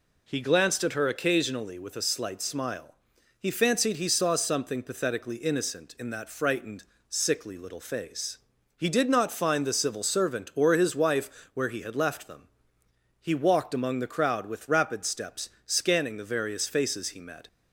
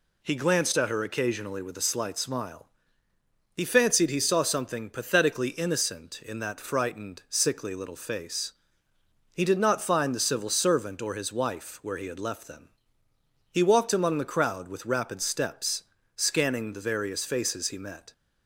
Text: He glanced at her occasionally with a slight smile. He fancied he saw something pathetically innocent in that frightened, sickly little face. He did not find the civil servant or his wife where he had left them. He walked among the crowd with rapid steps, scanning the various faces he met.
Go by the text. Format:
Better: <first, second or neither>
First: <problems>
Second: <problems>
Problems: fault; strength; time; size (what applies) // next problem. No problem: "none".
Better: neither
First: none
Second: none